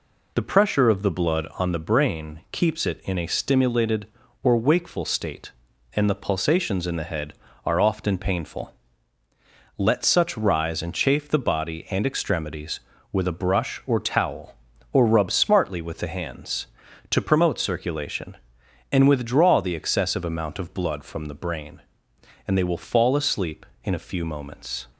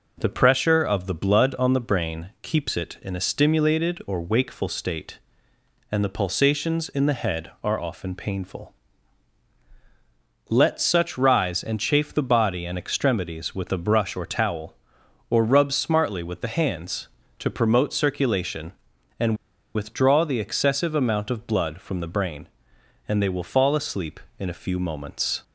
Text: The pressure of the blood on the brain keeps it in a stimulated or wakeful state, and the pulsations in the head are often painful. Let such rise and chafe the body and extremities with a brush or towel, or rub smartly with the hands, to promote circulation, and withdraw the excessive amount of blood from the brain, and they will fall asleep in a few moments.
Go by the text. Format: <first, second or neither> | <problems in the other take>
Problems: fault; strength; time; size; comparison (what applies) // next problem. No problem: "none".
first | pauses between "and" and "withdraw"; at 19.3 s; 0.38 s long